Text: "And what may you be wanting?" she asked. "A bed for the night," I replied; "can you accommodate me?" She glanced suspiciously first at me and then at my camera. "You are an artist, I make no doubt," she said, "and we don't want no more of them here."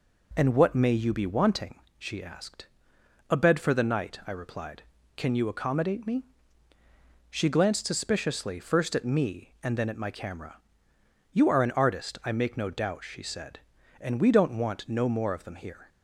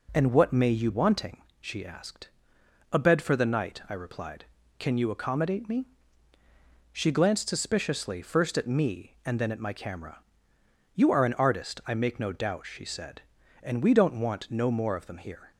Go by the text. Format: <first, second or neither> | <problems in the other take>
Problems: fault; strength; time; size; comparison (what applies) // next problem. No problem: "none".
first | skips "be"; at 0.9 s